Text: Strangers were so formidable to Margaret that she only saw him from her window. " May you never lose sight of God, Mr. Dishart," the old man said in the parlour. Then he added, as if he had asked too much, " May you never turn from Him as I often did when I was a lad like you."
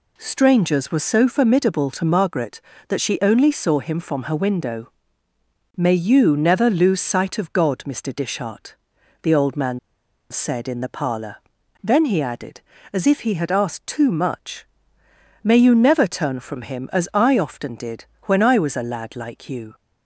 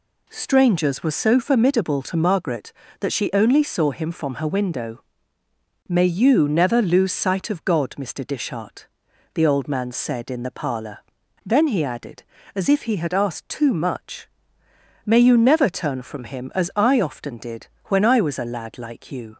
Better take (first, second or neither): second